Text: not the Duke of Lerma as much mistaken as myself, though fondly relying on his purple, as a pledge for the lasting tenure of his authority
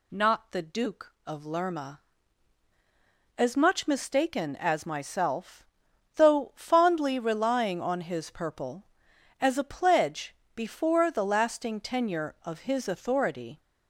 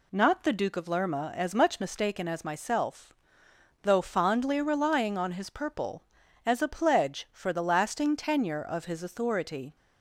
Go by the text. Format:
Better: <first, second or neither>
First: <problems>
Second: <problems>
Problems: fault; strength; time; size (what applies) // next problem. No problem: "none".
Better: second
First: says "before" for "for"; at 10.5 s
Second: none